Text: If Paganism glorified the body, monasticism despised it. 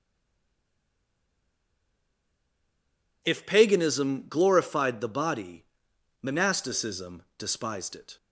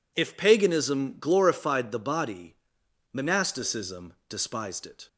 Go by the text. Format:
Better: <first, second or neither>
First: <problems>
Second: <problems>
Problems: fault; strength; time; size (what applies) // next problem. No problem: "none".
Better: second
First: stays silent before the first word; strong; until 3.2 s; 3.2 s long // pauses between "monasticism" and "despised"; slight; at 7.2 s; 0.16 s long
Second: pauses between "monasticism" and "despised"; slight; at 4.1 s; 0.16 s long